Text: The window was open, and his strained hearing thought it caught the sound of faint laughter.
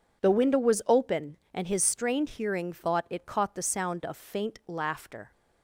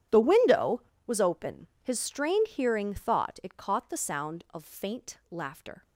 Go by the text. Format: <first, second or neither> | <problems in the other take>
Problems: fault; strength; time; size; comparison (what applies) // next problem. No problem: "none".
first | starts louder than the rest; strong; until 1.3 s; 10 dB // skips "and"; at 1.7 s